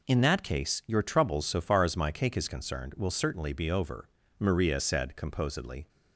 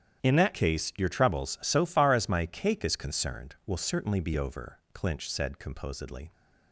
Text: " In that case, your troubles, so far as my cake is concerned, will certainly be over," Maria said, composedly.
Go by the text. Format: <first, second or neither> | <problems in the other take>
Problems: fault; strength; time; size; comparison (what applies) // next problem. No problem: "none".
first | starts louder than the rest; strong; until 1.2 s; 10.5 dB // says "Clinch" for "Maria"; at 4.9 s